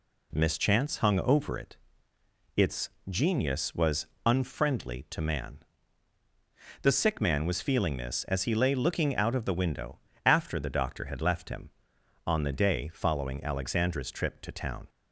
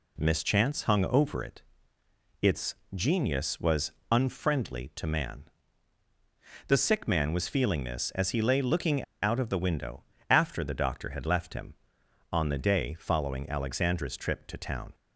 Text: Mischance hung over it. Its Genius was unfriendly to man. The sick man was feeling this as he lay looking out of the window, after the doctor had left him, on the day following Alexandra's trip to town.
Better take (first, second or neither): first